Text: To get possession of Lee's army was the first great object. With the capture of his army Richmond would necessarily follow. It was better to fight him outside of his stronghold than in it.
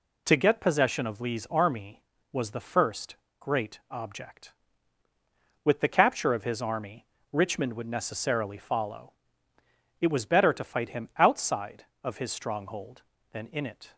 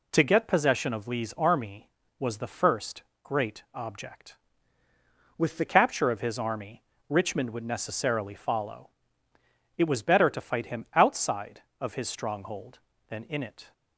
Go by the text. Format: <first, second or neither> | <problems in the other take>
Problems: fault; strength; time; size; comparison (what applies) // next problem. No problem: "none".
first | pauses between "first" and "great"; slight; at 3.0 s; 0.20 s long; slight in the first // changes voice from "With" to "the"; from 5.3 to 5.6 s; 0.3 s long // pauses between "army" and "Richmond"; slight; at 6.8 s; 0.26 s long; slight in the first